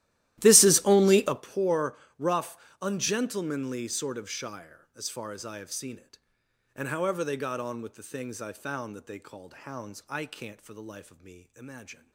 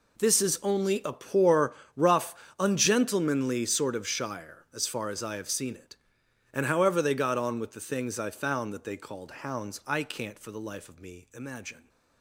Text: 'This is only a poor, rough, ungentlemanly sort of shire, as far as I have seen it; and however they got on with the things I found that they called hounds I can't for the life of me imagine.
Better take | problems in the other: second | starts louder than the rest; strong; until 1.6 s; 15 dB

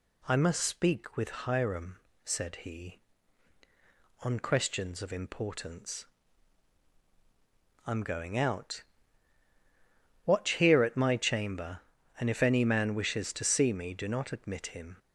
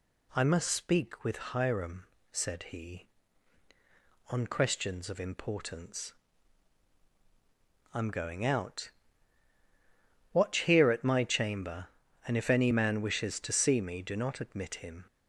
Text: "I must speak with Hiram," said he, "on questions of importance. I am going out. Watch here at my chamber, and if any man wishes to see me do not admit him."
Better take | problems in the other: neither | none

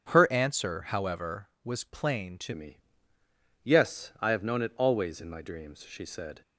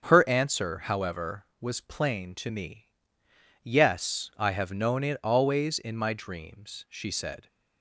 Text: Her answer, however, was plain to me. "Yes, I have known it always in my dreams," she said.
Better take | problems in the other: second | starts louder than the rest; until 1.1 s; 7 dB; also in the second // changes voice at "me"; from 2.5 s on; 3.9 s long

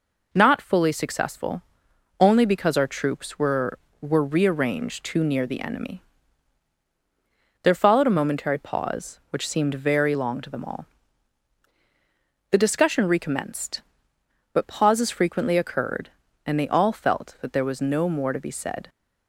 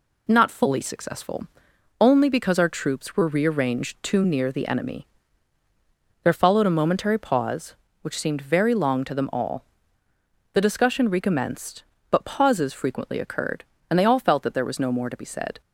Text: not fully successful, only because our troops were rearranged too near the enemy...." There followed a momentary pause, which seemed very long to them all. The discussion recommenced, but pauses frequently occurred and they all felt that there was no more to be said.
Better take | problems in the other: second | says "were" twice; at 3.9 s

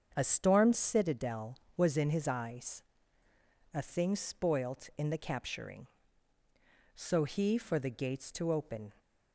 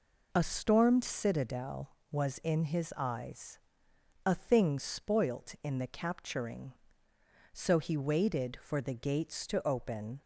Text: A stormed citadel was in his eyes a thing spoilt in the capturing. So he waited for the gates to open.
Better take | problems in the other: second | starts louder than the rest; strong; until 1.1 s; 7 dB // pauses between "eyes" and "a"; noticeable; at 2.8 s; 0.90 s long; noticeable in the second // skips "waited"; at 7.5 s

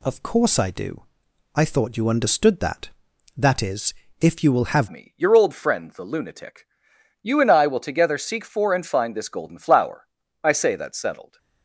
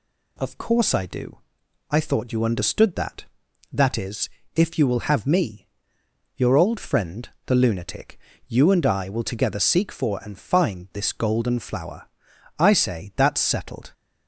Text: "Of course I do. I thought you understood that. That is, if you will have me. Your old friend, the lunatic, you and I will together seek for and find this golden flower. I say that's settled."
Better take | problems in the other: second | changes voice at "me"; from 4.8 s on; 6.5 s long

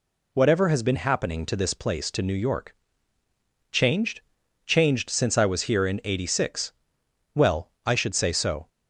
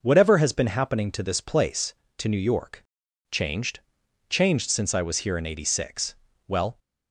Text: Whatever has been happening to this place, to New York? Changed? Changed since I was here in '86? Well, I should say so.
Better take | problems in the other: first | stops before "I should say so"; at 6.7 s

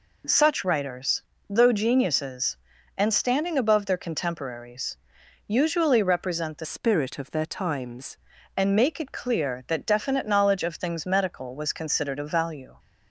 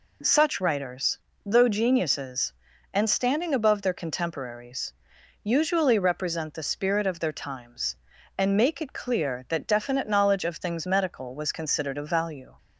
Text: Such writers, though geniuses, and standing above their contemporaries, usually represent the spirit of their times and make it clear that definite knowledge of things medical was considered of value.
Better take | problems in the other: second | changes voice from "spirit" to "times"; from 6.6 to 8.1 s; 1.5 s long

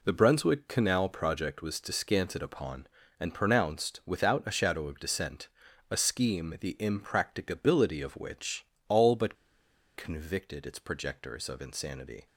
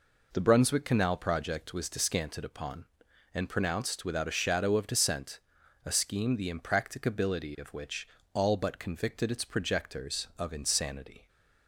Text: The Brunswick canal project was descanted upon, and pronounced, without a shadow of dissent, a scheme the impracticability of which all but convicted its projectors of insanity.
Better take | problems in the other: second | pauses between "which" and "all"; slight; at 8.6 s; 0.22 s long; slight in the second // pauses between "but" and "convicted"; noticeable; at 9.3 s; 0.60 s long

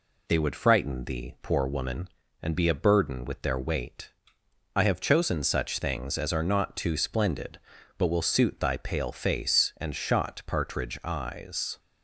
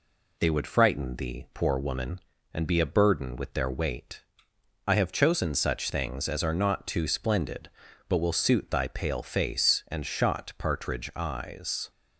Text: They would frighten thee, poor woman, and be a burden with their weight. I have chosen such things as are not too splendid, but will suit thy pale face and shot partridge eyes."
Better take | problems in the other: neither | none

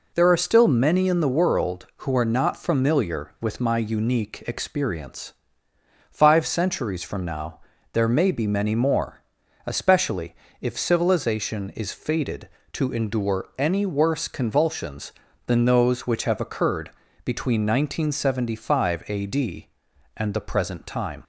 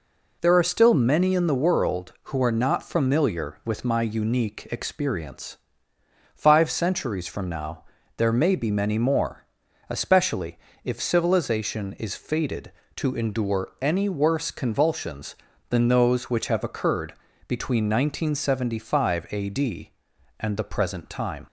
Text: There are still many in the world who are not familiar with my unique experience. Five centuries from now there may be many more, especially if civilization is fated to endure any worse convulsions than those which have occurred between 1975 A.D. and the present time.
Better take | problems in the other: neither | pauses between "now" and "there"; slight; the same in both // pauses between "especially" and "if"; slight; the same in both // pauses between "occurred" and "between"; slight; the same in both

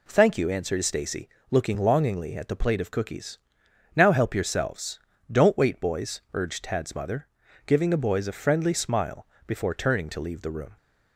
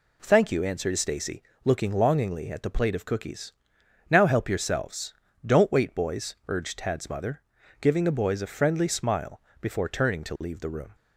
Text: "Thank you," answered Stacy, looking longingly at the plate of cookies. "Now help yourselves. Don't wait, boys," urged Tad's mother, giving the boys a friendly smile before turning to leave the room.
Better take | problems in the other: neither | pauses between "smile" and "before"; slight; the same in both

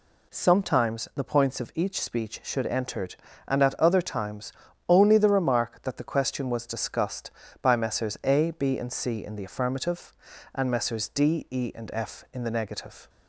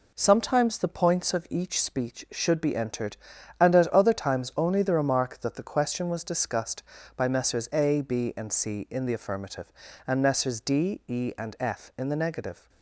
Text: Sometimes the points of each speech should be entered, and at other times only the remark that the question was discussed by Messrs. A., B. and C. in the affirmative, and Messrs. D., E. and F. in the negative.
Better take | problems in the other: second | skips "be"; at 2.6 s // pauses between "times" and "only"; slight; at 4.5 s; 0.34 s long

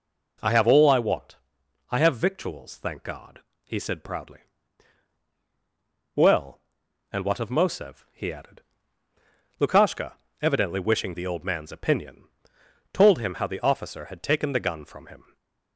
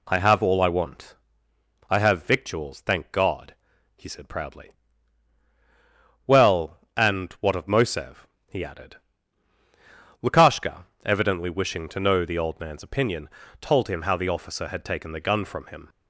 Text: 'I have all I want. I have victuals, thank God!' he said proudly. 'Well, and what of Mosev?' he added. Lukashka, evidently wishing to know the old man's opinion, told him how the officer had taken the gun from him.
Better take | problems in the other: second | skips "to know"; at 11.1 s // stays silent after the last word; slight; from 15.2 s on; 0.5 s long

